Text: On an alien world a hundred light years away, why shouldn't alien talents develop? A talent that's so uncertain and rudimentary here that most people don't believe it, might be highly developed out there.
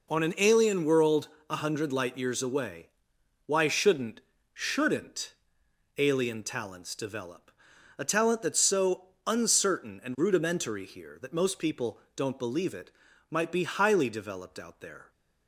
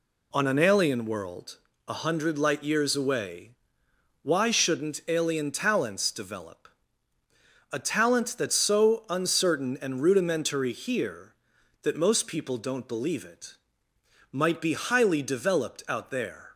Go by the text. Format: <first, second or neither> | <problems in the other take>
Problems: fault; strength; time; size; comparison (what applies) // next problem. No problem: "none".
second | pauses between "world" and "a"; slight; at 1.2 s; 0.22 s long; slight in the second // says "shouldn't" twice; at 4.5 s // pauses between "so" and "uncertain"; slight; at 9.0 s; 0.18 s long // pauses between "people" and "don't"; slight; at 12.0 s; 0.16 s long